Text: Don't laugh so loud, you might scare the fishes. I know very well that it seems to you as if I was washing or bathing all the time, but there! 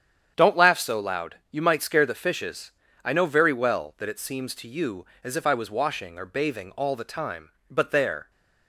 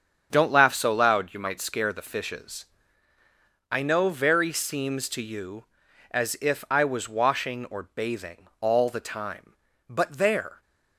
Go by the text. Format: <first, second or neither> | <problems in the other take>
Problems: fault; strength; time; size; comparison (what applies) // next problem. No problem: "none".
first | starts louder than the rest; strong; until 1.3 s; 7.5 dB; strong in the first // skips "well that it"; at 4.5 s